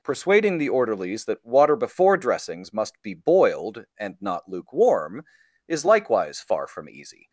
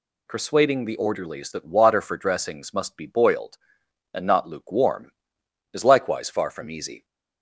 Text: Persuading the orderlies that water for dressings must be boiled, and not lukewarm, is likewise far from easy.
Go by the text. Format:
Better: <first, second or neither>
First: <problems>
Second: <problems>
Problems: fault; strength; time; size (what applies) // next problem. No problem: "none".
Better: second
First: says "before" for "for"; at 1.7 s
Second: none